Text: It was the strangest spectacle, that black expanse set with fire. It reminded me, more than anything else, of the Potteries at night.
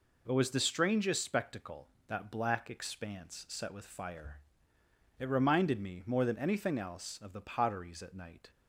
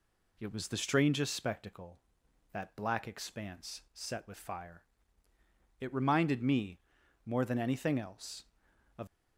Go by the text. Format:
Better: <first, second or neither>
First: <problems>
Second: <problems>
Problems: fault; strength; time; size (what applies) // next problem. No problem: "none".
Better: first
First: none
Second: stops before "the Potteries at night"; at 9.0 s